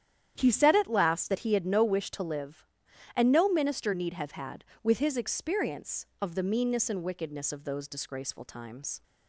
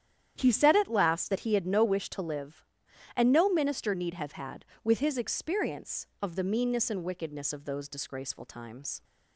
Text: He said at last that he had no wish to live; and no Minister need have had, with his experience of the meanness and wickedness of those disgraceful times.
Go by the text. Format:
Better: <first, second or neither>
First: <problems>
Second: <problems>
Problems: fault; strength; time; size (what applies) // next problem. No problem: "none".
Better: neither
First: starts louder than the rest; strong; until 1.3 s; 10 dB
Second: starts louder than the rest; strong; until 1.3 s; 10 dB